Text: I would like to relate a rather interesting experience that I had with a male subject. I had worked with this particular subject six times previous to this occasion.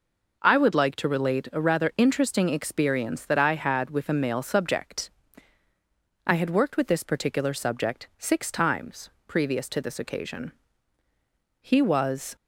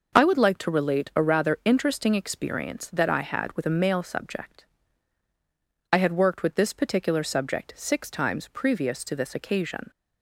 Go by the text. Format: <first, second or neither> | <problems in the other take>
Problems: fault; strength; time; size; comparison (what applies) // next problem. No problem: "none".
second | pauses between "times" and "previous"; slight; at 9.0 s; 0.18 s long // goes on to say "He was"; noticeable; from 11.6 s on; 0.74 s long